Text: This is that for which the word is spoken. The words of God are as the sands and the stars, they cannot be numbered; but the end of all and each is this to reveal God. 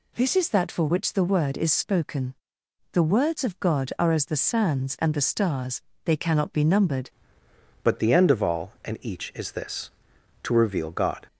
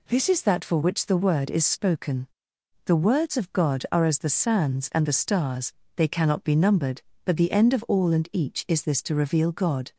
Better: second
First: changes voice at "but"; from 7.8 s on; 3.4 s long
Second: none

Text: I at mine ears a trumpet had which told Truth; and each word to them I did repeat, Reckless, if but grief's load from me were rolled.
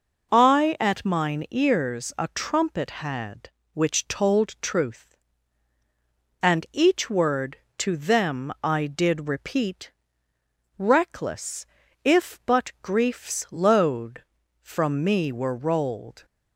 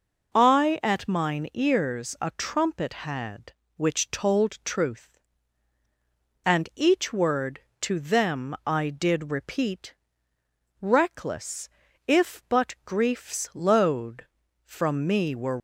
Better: first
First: none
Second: stops before "rolled"; at 15.5 s

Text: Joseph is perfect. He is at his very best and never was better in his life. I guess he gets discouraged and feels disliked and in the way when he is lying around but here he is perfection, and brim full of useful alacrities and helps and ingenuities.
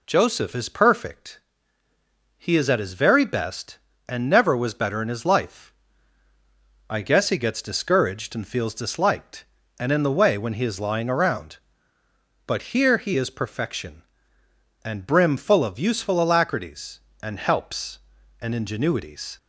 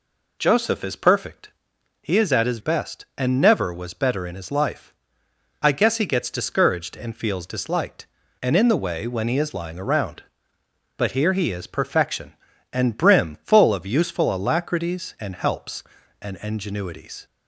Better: first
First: none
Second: skips "very"; at 2.5 s

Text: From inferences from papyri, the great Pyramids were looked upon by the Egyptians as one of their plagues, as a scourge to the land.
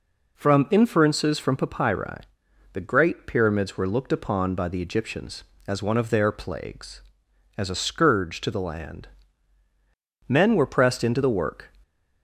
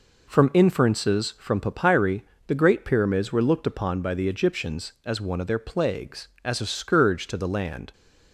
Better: second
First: goes on to say "Men were pressed into the work"; from 10.2 s on; 1.4 s long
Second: none

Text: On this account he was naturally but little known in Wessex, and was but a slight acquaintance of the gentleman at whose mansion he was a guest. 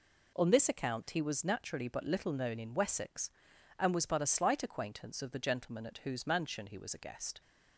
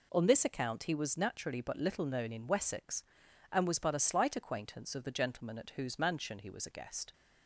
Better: neither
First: none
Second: none

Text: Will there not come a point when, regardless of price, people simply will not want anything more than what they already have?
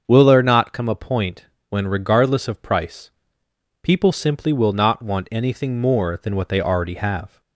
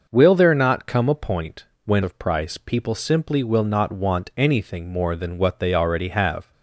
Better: first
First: starts louder than the rest; until 1.0 s; 6.5 dB // pauses between "point" and "when"; slight; at 1.4 s; 0.24 s long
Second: starts louder than the rest; until 1.1 s; 6 dB // pauses between "point" and "when"; slight; at 1.6 s; 0.18 s long // skips "regardless"; at 2.0 s

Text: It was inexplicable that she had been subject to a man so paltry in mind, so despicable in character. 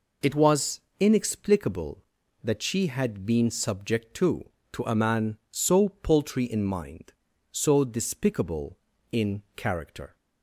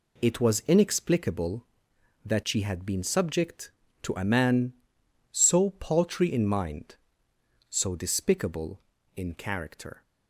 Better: second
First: pauses between "was" and "inexplicable"; slight; at 0.8 s; 0.18 s long // says "to" twice; at 4.7 s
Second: none

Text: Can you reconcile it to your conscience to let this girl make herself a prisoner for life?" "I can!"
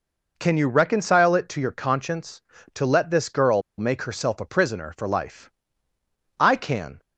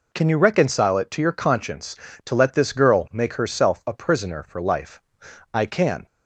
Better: second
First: pauses between "girl" and "make"; slight; at 3.6 s; 0.18 s long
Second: none

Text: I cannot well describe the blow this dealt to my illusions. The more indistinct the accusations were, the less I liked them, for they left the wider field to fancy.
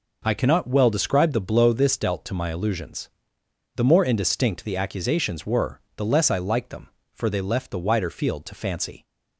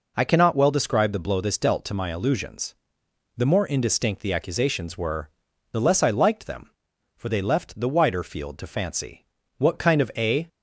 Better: first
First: none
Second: goes on to say "What kind of a"; noticeable; from 9.5 s on; 0.90 s long

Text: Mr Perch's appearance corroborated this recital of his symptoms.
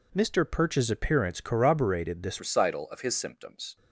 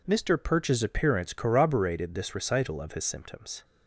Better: second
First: changes voice at "recital"; from 2.3 s on; 1.4 s long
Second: none

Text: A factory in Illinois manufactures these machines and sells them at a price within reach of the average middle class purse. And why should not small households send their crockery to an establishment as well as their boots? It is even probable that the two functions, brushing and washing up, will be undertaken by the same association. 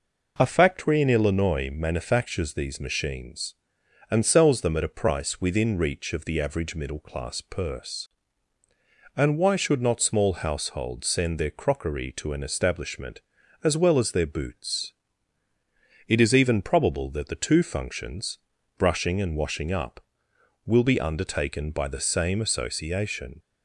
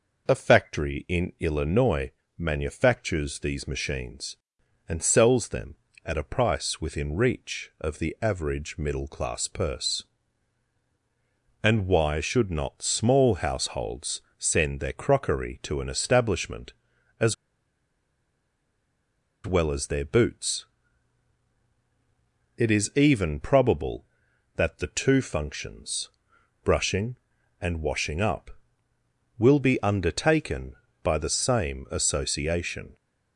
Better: first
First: none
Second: pauses between "Illinois" and "manufactures"; slight; at 2.0 s; 0.26 s long // pauses between "households" and "send"; slight; at 14.2 s; 0.18 s long // pauses between "as" and "well"; strong; at 17.3 s; 2.1 s long

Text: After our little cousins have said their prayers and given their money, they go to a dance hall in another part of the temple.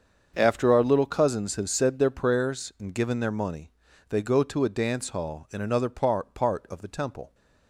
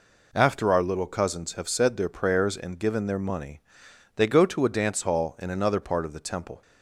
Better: second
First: starts louder than the rest; until 1.3 s; 7 dB // says "part" twice; at 6.3 s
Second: none

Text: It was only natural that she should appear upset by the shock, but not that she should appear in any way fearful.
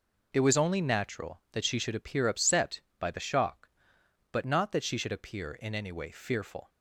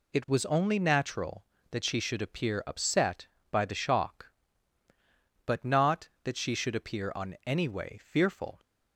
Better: first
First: none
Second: says "on" for "in"; at 7.1 s

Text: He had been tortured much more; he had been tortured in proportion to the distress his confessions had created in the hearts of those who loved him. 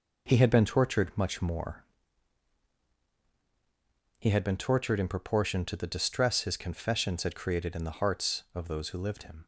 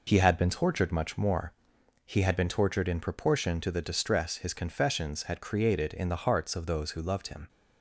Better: second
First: says "lived" for "loved"; at 8.9 s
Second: none

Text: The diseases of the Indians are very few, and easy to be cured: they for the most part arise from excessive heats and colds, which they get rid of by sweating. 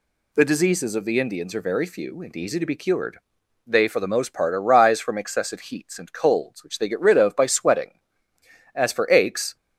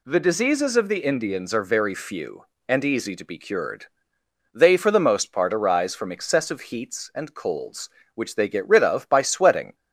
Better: second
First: goes on to say "As for aches"; noticeable; from 8.7 s on; 0.82 s long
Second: none

